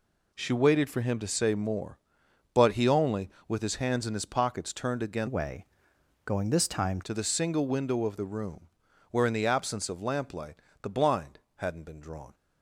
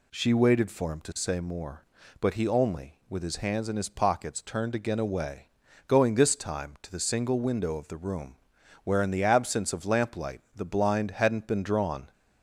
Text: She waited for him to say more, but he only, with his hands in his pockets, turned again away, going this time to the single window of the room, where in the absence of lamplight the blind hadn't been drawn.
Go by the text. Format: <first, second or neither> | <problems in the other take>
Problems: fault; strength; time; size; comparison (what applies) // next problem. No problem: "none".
second | changes voice from "away" to "time"; from 5.2 to 6.9 s; 1.7 s long // pauses between "lamplight" and "the"; slight; at 10.5 s; 0.26 s long // pauses between "blind" and "hadn't"; slight; at 11.3 s; 0.18 s long